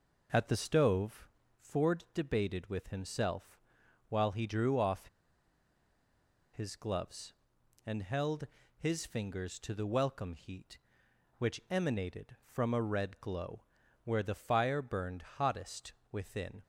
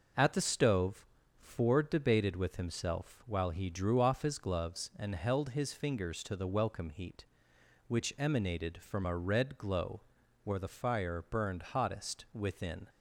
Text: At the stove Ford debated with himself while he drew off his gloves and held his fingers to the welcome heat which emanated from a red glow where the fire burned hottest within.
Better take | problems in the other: second | pauses between "stove" and "Ford"; slight; at 1.2 s; 0.32 s long; slight in the second // pauses between "himself" and "while"; noticeable; at 3.5 s; 0.48 s long // pauses between "off" and "his"; strong; at 5.0 s; 1.4 s long // pauses between "held" and "his"; slight; at 8.4 s; 0.32 s long // pauses between "glow" and "where"; at 13.6 s; 0.42 s long; also in the second // pauses between "burned" and "hottest"; slight; at 15.2 s; 0.16 s long // pauses between "hottest" and "within"; slight; at 15.9 s; 0.22 s long

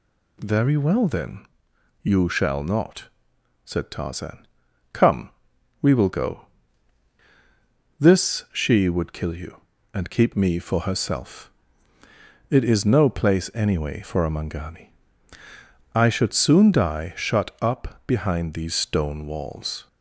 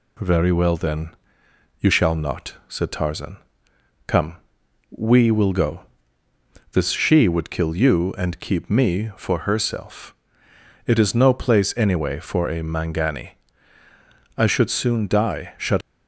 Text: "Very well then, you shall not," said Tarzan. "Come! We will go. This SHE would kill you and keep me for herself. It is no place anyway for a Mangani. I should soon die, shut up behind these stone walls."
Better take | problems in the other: first | stops before "up behind these stone walls"; at 15.8 s

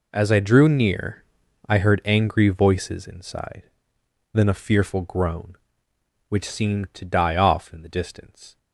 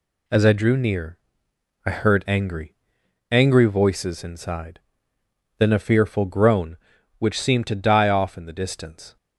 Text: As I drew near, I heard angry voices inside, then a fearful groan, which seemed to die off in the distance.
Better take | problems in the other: first | says "angry" twice; at 3.2 s

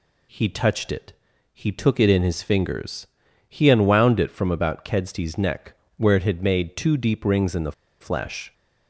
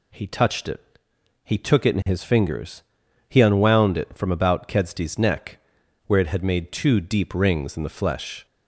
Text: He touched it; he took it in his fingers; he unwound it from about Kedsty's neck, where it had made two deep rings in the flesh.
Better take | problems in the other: second | pauses between "the" and "flesh"; slight; at 7.7 s; 0.27 s long

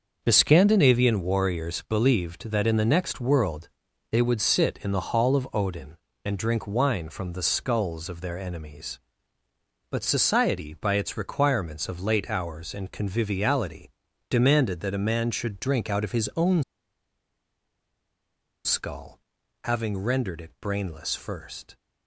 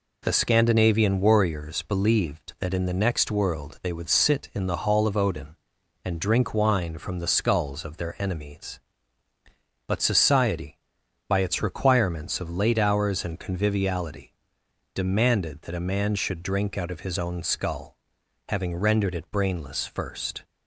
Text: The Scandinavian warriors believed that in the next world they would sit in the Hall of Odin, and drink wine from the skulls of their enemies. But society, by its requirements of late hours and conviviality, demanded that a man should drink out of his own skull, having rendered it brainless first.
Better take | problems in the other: second | starts louder than the rest; until 1.2 s; 6 dB // pauses between "world" and "they"; at 3.6 s; 0.44 s long // pauses between "own" and "skull"; strong; at 16.6 s; 2.0 s long

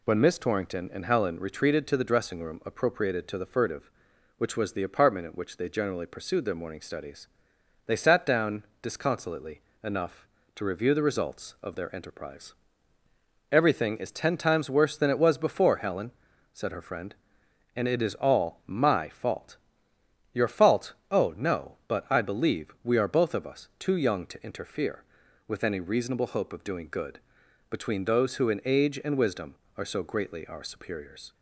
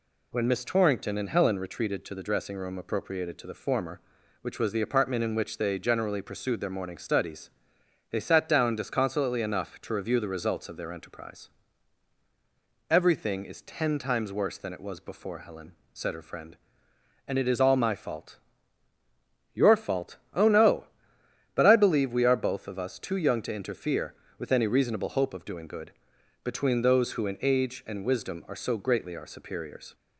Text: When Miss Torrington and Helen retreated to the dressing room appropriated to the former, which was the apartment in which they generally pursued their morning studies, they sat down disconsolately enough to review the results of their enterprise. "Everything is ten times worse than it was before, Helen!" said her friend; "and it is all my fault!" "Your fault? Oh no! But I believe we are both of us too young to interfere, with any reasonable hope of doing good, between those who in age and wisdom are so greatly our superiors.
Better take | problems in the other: second | says "furtive" for "former"; at 3.4 s // pauses between "down" and "disconsolately"; slight; at 8.6 s; 0.16 s long // pauses between "disconsolately" and "enough"; slight; at 9.6 s; 0.20 s long

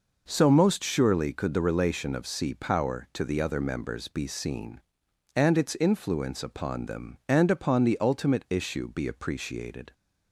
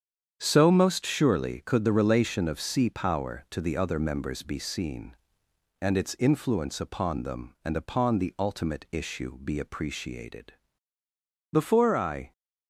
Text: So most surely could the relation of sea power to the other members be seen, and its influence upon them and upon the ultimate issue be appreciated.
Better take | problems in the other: first | starts louder than the rest; strong; until 1.3 s; 8 dB // goes on to say "Before I"; noticeable; from 11.5 s on; 0.80 s long

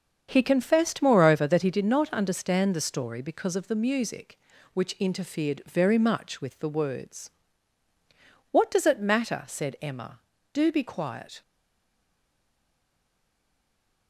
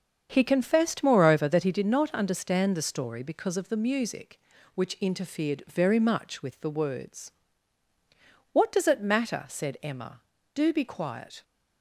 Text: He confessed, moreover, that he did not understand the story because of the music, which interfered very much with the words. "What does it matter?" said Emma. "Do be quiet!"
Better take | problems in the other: second | starts louder than the rest; strong; until 1.3 s; 7 dB; also in the second // stays silent after the last word; strong; from 11.4 s on; 2.6 s long

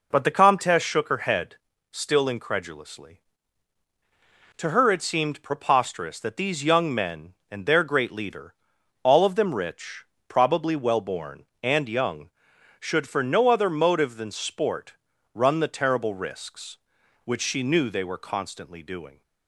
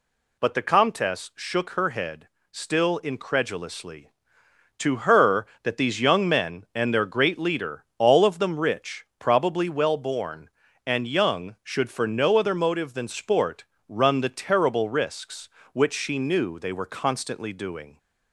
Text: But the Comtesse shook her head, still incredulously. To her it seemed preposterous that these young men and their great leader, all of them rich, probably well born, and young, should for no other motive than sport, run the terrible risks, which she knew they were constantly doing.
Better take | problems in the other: first | skips "it seemed preposterous"; at 5.5 s

